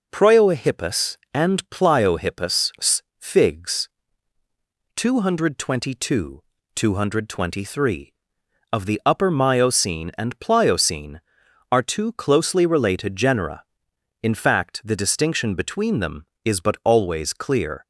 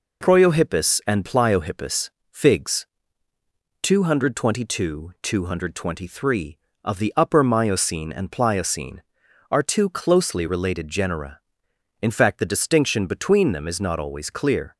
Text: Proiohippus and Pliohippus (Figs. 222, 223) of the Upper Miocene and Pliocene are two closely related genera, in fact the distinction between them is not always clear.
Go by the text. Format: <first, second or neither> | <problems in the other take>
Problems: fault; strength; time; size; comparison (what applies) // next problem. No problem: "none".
second | says "but" for "not"; at 16.6 s